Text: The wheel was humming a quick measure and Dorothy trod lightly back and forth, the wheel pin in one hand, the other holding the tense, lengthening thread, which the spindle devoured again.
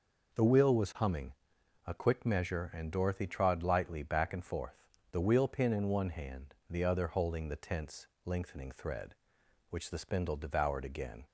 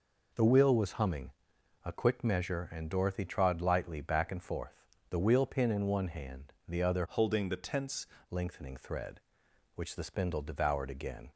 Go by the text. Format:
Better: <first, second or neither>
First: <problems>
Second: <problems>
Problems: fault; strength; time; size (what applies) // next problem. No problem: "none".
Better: first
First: pauses between "humming" and "a"; noticeable; at 1.3 s; 0.52 s long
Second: pauses between "humming" and "a"; noticeable; at 1.3 s; 0.52 s long // changes voice from "holding" to "tense"; from 7.0 to 8.0 s; 1.0 s long